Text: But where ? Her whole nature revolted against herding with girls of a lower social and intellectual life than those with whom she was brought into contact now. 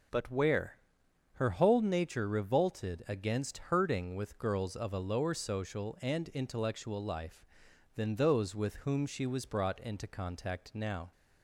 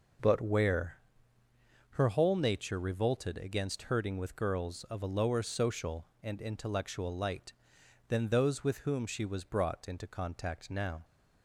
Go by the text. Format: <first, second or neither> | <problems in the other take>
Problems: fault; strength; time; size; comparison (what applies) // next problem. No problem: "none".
first | says "light" for "life"; at 7.1 s